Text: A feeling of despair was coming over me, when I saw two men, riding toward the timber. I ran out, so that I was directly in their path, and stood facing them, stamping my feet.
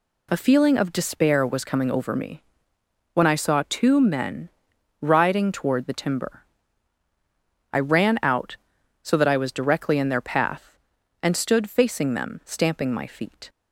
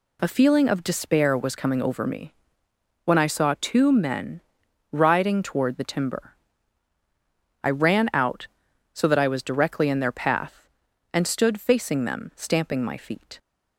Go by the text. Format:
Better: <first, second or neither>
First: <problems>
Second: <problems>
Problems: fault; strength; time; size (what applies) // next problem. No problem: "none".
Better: neither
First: none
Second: none